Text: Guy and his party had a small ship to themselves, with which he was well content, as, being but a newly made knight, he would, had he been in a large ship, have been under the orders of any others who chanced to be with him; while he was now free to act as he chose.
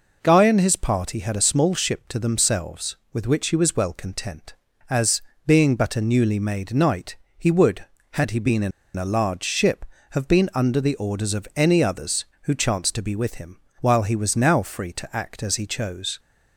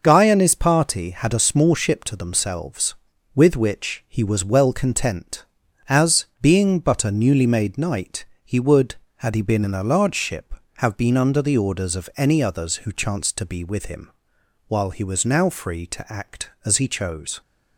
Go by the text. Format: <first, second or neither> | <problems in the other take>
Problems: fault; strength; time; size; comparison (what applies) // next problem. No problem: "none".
second | pauses between "in" and "a"; slight; at 8.7 s; 0.26 s long